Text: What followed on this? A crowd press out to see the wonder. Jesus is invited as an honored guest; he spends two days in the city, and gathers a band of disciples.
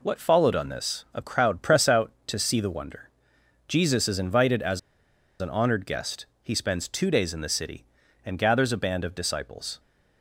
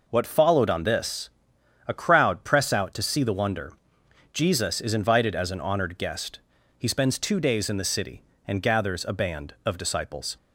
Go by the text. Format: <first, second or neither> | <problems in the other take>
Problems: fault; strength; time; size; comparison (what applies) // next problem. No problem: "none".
second | pauses between "as" and "an"; noticeable; at 4.7 s; 0.61 s long